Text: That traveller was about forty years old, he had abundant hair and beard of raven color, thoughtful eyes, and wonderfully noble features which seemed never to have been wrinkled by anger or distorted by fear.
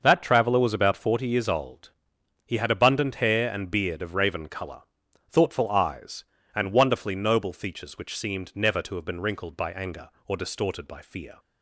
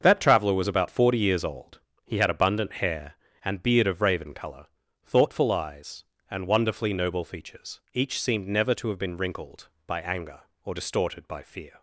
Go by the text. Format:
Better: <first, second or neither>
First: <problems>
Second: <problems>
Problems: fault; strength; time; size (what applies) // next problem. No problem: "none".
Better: first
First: none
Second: starts louder than the rest; until 1.0 s; 6.5 dB // says "each" for "which"; at 7.9 s